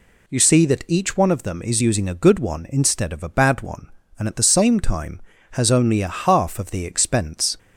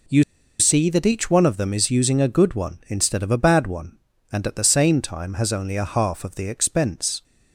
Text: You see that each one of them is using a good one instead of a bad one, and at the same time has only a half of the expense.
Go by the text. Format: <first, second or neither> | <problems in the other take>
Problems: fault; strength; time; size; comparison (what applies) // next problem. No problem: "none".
first | pauses between "You" and "see"; at 0.2 s; 0.36 s long